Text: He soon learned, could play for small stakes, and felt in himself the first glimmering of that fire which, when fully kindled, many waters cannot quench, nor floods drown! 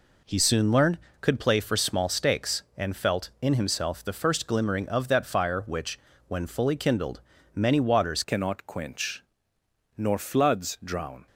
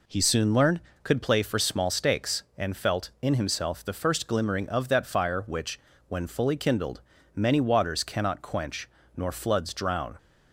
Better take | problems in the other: second | changes voice at "cannot"; from 8.2 s on; 3.0 s long

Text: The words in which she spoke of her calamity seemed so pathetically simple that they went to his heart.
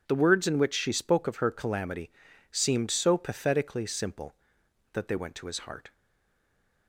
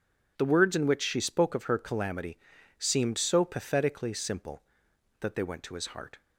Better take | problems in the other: second | pauses between "calamity" and "seemed"; at 2.0 s; 0.42 s long; also in the second // stays silent after the last word; from 5.9 s on; 0.9 s long

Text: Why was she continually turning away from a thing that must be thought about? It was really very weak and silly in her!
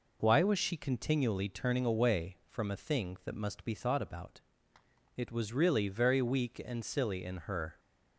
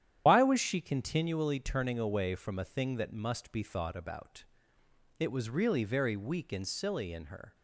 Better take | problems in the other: first | loses the start of "Why"; at 0.2 s; 110 ms // starts louder than the rest; strong; until 1.2 s; 10.5 dB

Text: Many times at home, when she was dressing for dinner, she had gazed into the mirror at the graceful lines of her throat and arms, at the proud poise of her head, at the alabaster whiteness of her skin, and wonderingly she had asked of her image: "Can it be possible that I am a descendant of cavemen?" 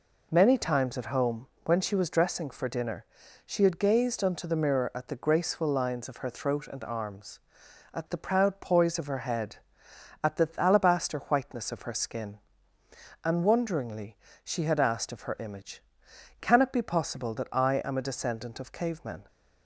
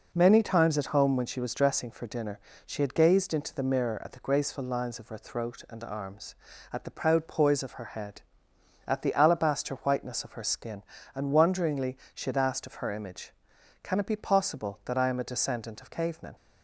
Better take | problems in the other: second | says "unto" for "into"; at 4.2 s // pauses between "wonderingly" and "she"; slight; at 14.1 s; 0.28 s long; slight in the second

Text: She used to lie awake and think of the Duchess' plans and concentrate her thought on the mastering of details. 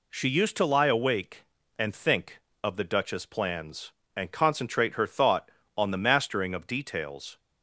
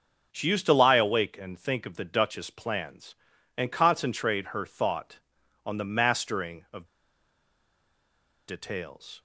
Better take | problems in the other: first | starts louder than the rest; noticeable; until 1.3 s; 6 dB // pauses between "of" and "details"; strong; at 6.8 s; 1.6 s long

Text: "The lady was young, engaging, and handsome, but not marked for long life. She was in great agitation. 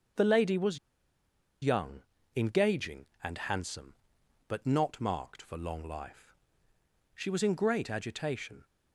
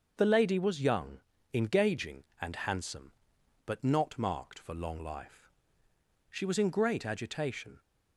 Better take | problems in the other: second | starts louder than the rest; until 2.3 s; 6 dB; also in the second // pauses between "was" and "young"; noticeable; at 0.7 s; 0.86 s long

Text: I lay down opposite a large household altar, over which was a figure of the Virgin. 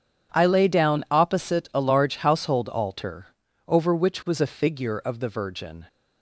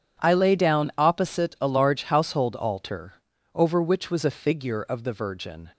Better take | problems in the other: neither | none

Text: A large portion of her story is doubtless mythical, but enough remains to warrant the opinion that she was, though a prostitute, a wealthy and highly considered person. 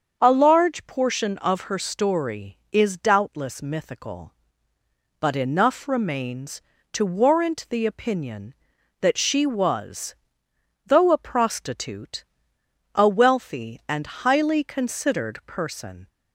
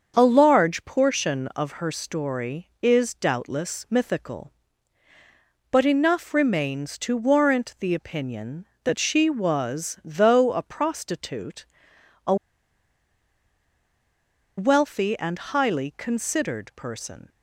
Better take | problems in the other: first | starts louder than the rest; until 1.1 s; 7 dB; also in the first // pauses between "a" and "wealthy"; strong; at 12.3 s; 2.2 s long

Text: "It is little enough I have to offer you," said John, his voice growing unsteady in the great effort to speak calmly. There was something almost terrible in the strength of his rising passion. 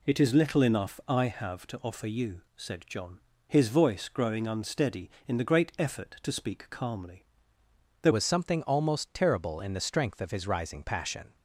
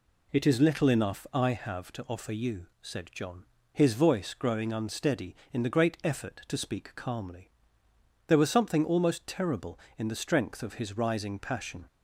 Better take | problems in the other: second | changes voice at "was"; from 8.1 s on; 3.2 s long

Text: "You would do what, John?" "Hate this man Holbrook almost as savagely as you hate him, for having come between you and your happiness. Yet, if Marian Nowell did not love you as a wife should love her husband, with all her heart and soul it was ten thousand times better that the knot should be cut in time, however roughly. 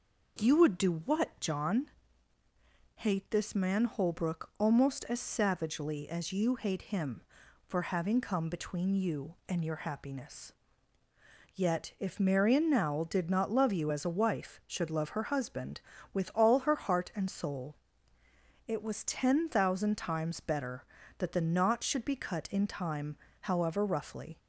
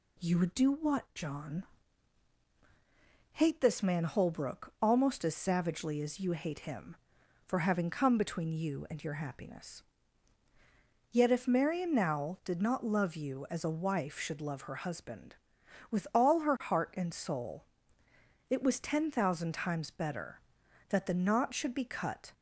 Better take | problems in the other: first | pauses between "soul" and "it"; noticeable; at 17.6 s; 0.86 s long; noticeable in the first // stops before "in time however roughly"; at 22.3 s

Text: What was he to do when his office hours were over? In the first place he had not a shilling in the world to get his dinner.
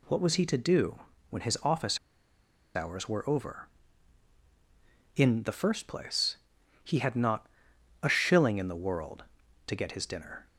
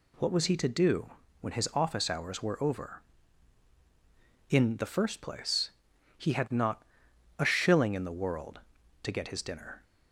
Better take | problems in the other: second | pauses between "do" and "when"; slight; at 0.9 s; 0.30 s long; slight in the second // pauses between "office" and "hours"; noticeable; at 1.9 s; 0.77 s long // pauses between "place" and "he"; noticeable; at 6.3 s; 0.46 s long; noticeable in the second // pauses between "not" and "a"; noticeable; at 7.4 s; 0.56 s long; noticeable in the second

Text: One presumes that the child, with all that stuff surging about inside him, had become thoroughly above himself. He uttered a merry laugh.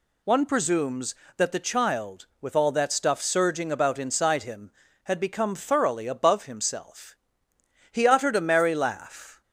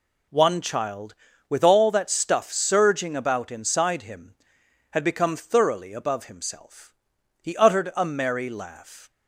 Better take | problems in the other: first | skips "presumes that the"; at 0.5 s

